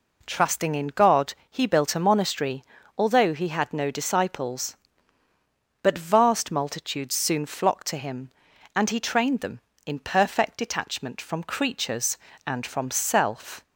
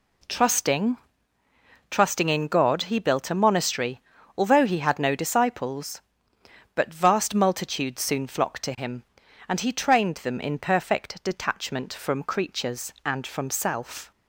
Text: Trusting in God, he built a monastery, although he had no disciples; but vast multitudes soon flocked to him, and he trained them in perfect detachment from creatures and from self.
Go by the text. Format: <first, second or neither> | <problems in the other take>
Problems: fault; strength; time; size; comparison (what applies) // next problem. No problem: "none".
first | says "Trusting" twice; at 1.9 s